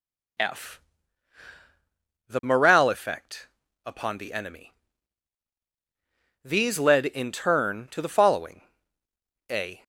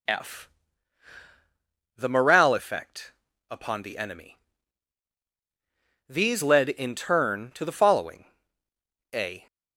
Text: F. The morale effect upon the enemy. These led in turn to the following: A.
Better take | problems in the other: neither | pauses between "effect" and "upon"; the same in both

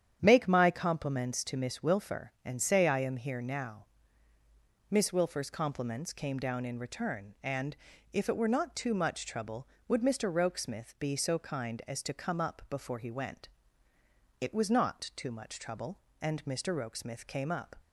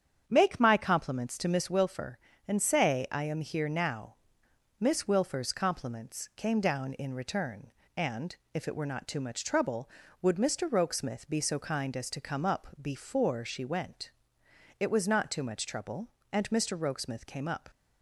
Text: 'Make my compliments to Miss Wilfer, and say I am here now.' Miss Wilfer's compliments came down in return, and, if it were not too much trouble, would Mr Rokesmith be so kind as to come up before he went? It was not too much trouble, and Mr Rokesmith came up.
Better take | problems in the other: first | starts louder than the rest; strong; until 1.2 s; 8 dB; strong in the first // pauses between "up" and "before"; slight; at 12.6 s; 0.16 s long // says "she" for "he"; at 13.4 s

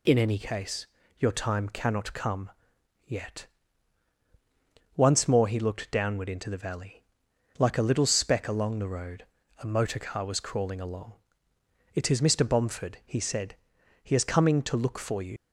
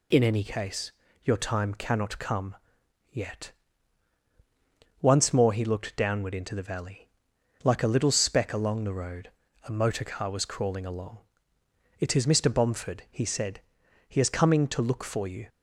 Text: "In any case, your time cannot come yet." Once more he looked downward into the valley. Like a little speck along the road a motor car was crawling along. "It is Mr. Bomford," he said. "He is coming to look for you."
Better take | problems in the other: second | pauses between "come" and "yet"; noticeable; at 2.5 s; 0.54 s long; noticeable in the second // pauses between "road" and "a"; slight; at 9.2 s; 0.34 s long; slight in the second // leaves "you" unfinished; at 15.3 s; 70 ms

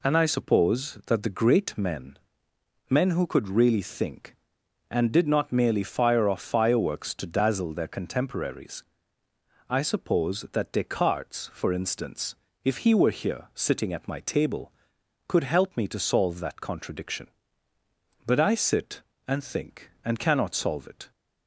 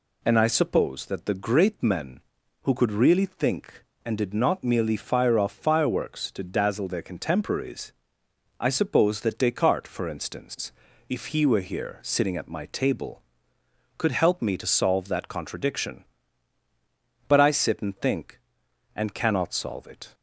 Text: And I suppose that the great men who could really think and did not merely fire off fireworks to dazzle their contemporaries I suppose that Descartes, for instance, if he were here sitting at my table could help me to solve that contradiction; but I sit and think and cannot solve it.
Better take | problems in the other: second | says "men" twice; at 2.8 s // pauses between "contemporaries" and "I"; noticeable; at 8.8 s; 0.86 s long; noticeable in the second

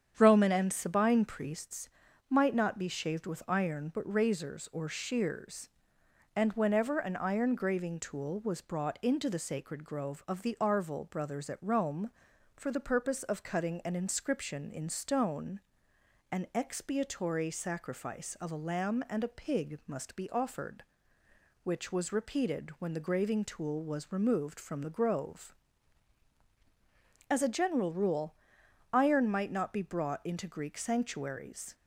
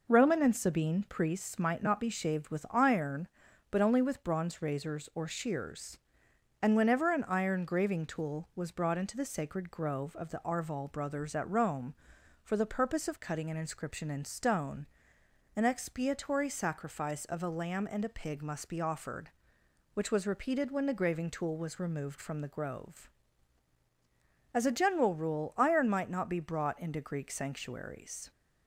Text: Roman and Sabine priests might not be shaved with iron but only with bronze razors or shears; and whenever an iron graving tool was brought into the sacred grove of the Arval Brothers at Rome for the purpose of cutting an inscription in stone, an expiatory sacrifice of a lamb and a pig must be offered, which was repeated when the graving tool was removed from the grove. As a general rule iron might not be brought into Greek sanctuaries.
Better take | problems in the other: second | starts louder than the rest; strong; until 1.1 s; 8.5 dB // pauses between "priests" and "might"; at 1.8 s; 0.40 s long // skips "only with bronze"; at 4.1 s // pauses between "rule" and "iron"; noticeable; at 28.3 s; 0.60 s long

